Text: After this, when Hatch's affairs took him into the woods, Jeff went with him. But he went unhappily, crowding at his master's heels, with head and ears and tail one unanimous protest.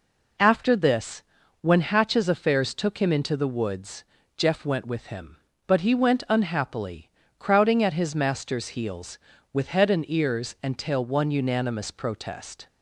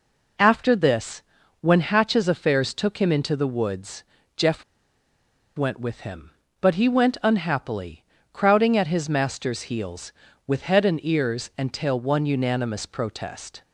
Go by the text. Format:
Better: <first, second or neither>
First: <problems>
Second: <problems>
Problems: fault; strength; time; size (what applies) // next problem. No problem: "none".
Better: first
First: none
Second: pauses between "Jeff" and "went"; noticeable; at 4.6 s; 0.93 s long